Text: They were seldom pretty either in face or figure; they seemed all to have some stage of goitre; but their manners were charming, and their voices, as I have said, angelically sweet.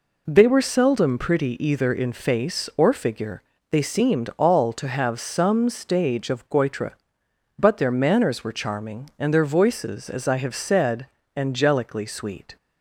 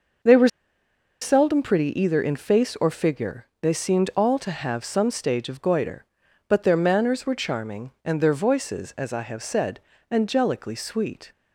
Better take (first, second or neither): first